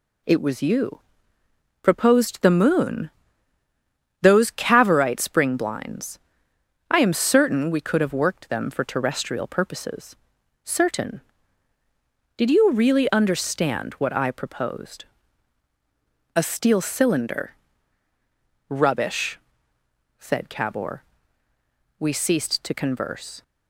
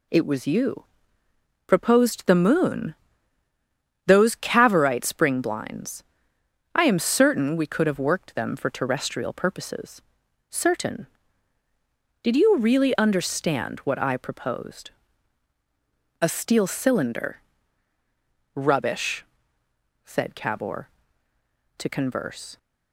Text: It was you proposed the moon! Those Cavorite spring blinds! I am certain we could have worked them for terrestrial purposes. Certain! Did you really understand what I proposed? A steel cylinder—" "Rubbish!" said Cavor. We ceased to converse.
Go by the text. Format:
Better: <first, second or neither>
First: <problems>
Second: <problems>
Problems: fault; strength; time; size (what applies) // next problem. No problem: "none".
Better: first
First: pauses between "you" and "proposed"; noticeable; at 0.9 s; 0.82 s long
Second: pauses between "you" and "proposed"; noticeable; at 0.8 s; 0.82 s long // skips "We ceased"; at 21.3 s